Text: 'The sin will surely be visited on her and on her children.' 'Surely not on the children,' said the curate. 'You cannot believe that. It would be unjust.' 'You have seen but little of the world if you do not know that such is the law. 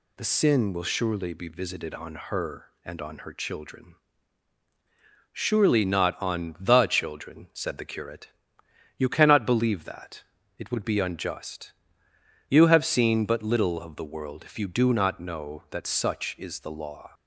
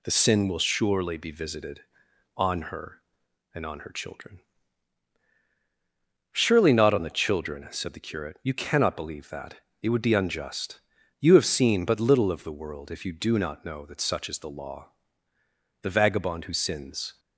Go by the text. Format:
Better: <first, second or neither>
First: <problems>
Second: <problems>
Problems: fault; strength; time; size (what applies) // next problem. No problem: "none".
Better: first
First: none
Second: goes on to say "The vagabond who sins"; from 15.8 s on; 1.3 s long